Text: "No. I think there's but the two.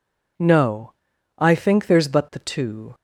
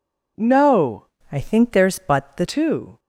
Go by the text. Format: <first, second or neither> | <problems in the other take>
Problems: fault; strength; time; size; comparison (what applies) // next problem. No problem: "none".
first | changes voice from "I" to "the"; from 1.3 to 2.4 s; 1.1 s long